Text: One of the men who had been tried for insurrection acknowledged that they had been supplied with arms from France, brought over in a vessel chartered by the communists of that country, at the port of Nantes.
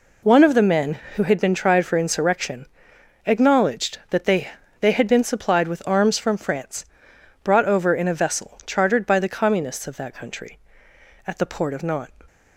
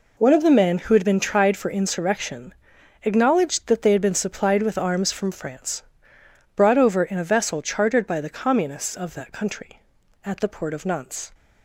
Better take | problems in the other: second | pauses between "insurrection" and "acknowledged"; noticeable; at 2.6 s; 0.60 s long; noticeable in the second // says "they" twice; at 4.7 s

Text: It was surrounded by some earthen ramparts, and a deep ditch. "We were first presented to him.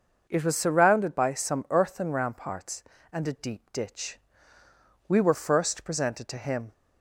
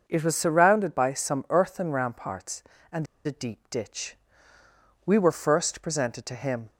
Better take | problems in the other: first | starts louder than the rest; noticeable; until 1.0 s; 6 dB; noticeable in the first // pauses between "and" and "a"; slight; at 3.0 s; 0.21 s long

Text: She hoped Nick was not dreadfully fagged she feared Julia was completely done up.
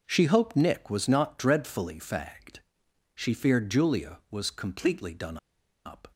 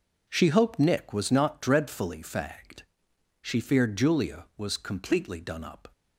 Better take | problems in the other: second | pauses between "fagged" and "she"; noticeable; at 2.5 s; 0.58 s long; noticeable in the second // pauses between "done" and "up"; noticeable; at 5.3 s; 0.48 s long

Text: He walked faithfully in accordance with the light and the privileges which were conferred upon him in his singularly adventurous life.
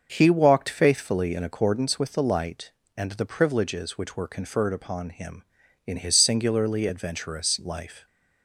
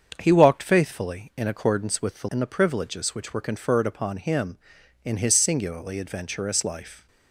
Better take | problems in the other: first | starts louder than the rest; strong; until 1.1 s; 7 dB; also in the first // skips "light"; at 2.2 s

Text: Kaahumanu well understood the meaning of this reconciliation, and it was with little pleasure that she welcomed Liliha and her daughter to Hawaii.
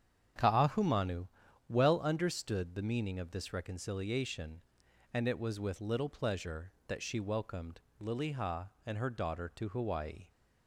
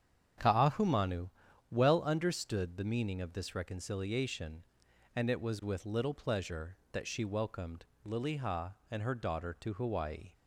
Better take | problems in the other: neither | starts louder than the rest; strong; the same in both // pauses between "Kaahumanu" and "well"; the same in both // pauses between "welcomed" and "Liliha"; slight; the same in both

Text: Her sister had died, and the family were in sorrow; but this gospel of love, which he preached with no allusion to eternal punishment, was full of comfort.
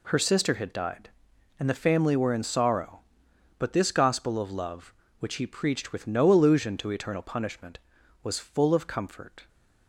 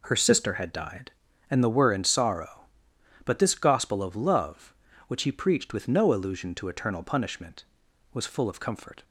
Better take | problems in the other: first | skips "family"; at 1.6 s

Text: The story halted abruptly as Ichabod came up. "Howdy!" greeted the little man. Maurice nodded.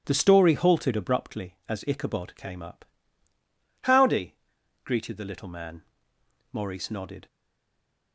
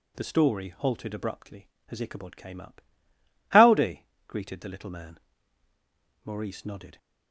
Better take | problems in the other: second | stays silent after the last word; slight; from 7.2 s on; 0.9 s long

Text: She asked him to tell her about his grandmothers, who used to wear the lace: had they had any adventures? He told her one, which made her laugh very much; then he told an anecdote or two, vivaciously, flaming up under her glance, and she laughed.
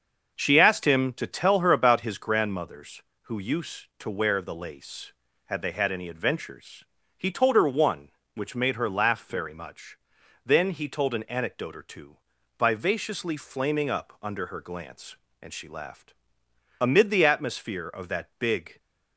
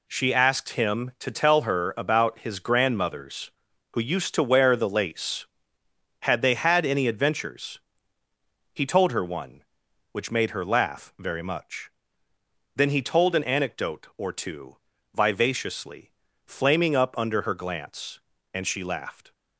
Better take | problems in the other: second | starts louder than the rest; until 1.3 s; 6.5 dB // goes on to say "Amid the atmosphere of that big"; strong; from 16.8 s on; 2.0 s long

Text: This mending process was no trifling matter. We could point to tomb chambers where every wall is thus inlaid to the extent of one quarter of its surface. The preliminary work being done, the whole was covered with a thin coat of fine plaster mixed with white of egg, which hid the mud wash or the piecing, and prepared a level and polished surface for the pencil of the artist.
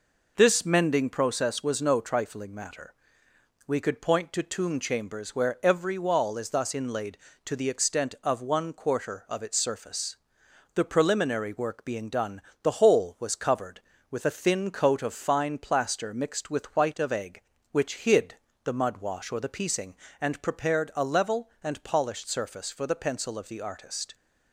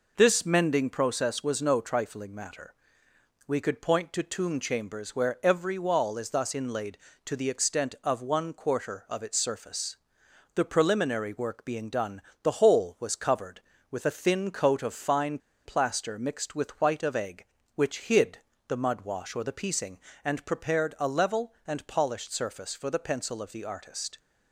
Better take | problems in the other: first | pauses between "fine" and "plaster"; slight; at 15.3 s; 0.27 s long // pauses between "hid" and "the"; slight; at 18.3 s; 0.30 s long; slight in the first

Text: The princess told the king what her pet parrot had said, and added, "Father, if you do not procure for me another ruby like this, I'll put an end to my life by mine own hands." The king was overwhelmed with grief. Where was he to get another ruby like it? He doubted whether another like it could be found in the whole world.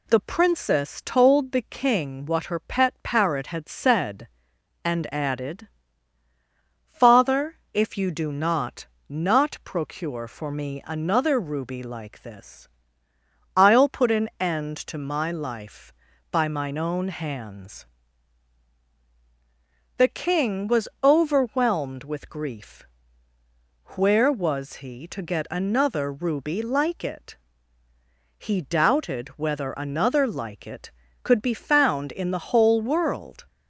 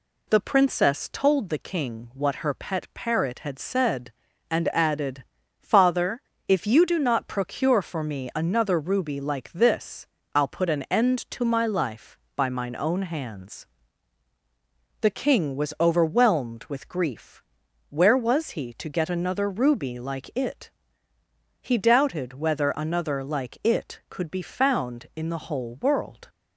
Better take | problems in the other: second | says "not" twice; at 9.0 s

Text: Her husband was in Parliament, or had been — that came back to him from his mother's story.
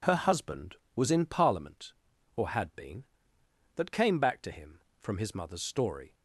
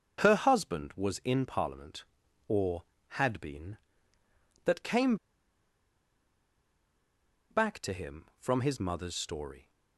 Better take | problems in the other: first | starts louder than the rest; until 1.2 s; 7 dB // pauses between "came" and "back"; strong; at 5.1 s; 2.3 s long

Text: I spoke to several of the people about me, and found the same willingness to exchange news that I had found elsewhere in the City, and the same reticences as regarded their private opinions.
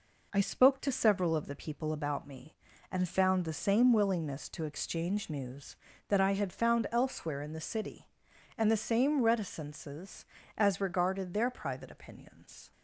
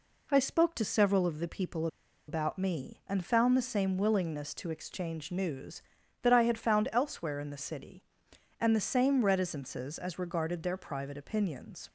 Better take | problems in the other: first | pauses between "people" and "about"; at 1.8 s; 0.41 s long

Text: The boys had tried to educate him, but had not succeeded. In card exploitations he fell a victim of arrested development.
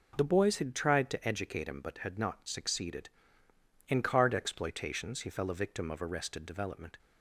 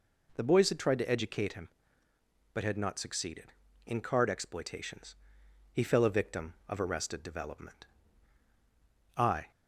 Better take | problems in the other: first | pauses between "exploitations" and "he"; noticeable; at 5.1 s; 0.58 s long // goes on to say "I"; slight; from 9.1 s on; 0.34 s long

